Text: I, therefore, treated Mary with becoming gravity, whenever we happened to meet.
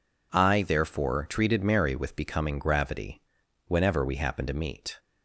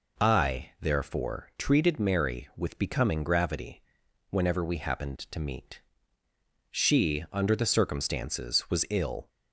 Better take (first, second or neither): first